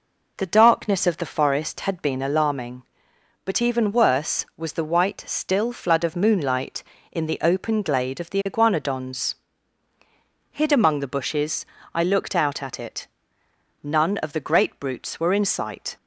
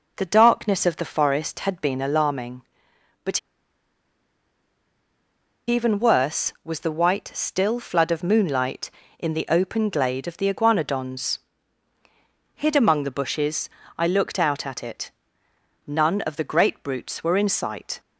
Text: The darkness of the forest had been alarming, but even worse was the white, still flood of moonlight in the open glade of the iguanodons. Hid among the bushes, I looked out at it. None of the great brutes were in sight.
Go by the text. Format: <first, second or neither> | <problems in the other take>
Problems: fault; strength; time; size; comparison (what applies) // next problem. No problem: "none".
first | pauses between "but" and "even"; strong; at 3.3 s; 2.2 s long